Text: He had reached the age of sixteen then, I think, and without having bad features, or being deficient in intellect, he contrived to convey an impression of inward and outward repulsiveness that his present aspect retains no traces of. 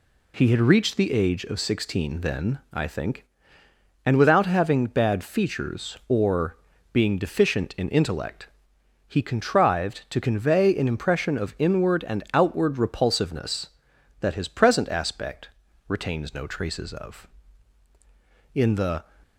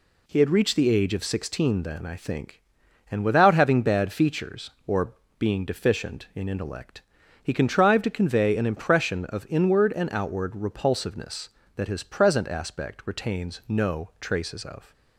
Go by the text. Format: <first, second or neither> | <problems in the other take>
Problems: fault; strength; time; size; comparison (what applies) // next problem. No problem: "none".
second | pauses between "or" and "being"; slight; at 6.5 s; 0.34 s long; slight in the second // pauses between "aspect" and "retains"; at 15.4 s; 0.40 s long // goes on to say "In the"; from 18.5 s on; 0.52 s long